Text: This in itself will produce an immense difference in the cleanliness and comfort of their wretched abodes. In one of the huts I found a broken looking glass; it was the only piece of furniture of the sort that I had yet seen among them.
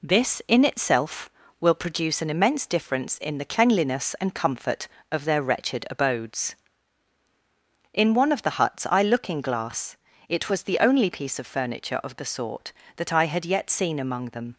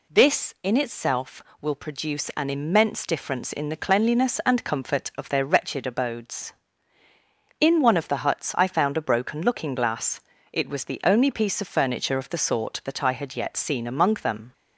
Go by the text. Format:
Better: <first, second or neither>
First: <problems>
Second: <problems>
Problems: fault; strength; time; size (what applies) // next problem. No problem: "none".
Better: second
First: skips "found a broken"; at 9.0 s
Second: none